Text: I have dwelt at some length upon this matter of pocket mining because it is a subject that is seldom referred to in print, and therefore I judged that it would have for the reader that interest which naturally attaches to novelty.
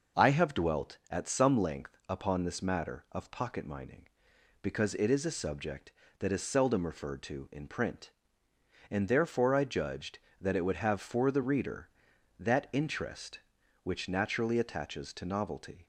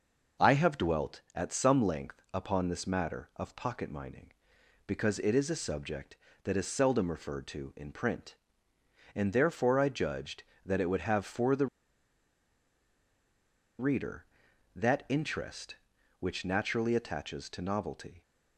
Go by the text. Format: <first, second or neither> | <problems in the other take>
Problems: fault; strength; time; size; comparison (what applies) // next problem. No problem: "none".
first | pauses between "the" and "reader"; strong; at 11.6 s; 2.1 s long